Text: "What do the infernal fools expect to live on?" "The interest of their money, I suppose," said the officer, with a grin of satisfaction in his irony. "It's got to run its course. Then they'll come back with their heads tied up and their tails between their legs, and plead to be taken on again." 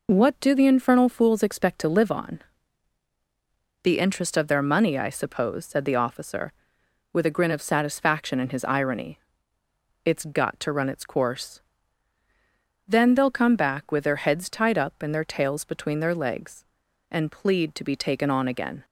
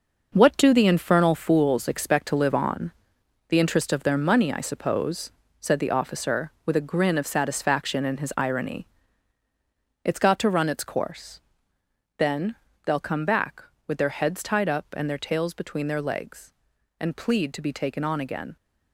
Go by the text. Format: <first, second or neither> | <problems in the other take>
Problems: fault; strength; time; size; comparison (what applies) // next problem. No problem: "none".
first | gets quieter; strong; throughout; 9 dB // pauses between "Then" and "they'll"; slight; at 12.5 s; 0.32 s long